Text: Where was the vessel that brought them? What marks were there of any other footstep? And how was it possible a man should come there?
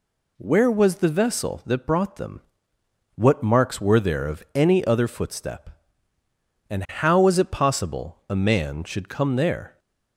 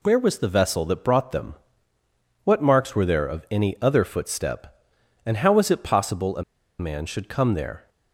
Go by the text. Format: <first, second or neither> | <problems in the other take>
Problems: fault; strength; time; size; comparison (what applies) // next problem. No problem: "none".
first | pauses between "a" and "man"; at 6.4 s; 0.36 s long